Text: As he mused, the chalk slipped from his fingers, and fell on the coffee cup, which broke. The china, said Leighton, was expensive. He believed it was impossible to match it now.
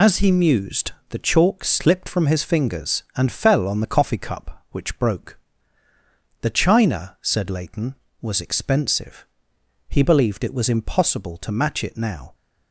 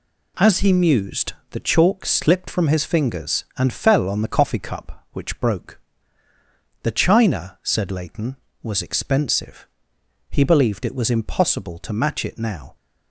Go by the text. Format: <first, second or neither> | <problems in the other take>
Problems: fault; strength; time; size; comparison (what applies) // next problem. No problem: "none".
second | loses the start of "As"; at 0.0 s; 50 ms